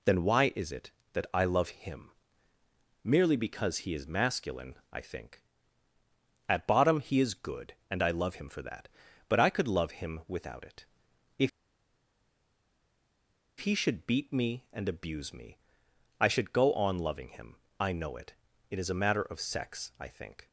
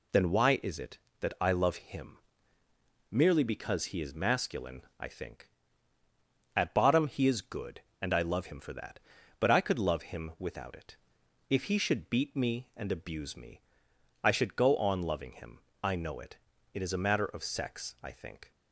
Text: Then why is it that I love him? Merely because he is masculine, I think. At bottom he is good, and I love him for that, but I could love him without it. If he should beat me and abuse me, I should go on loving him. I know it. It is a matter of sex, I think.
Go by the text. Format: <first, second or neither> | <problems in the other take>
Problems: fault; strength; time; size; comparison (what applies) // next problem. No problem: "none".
second | pauses between "If" and "he"; strong; at 11.4 s; 2.1 s long